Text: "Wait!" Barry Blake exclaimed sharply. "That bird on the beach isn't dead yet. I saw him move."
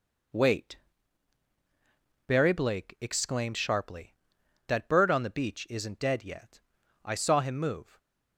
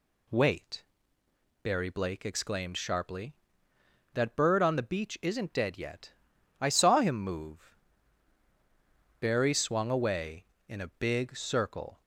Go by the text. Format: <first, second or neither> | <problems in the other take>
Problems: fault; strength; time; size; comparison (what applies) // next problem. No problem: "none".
first | goes on to say "Barry swung away in a big circle"; strong; from 9.2 s on; 2.8 s long